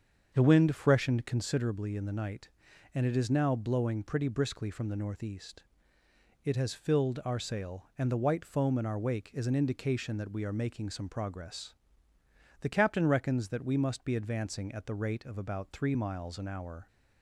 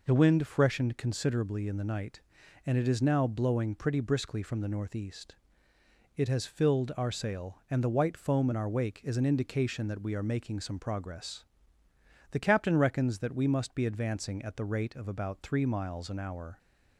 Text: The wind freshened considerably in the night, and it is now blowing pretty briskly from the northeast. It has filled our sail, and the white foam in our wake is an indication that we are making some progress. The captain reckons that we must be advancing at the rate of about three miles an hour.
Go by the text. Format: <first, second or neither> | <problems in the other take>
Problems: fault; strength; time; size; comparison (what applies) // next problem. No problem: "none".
second | starts louder than the rest; until 1.6 s; 7 dB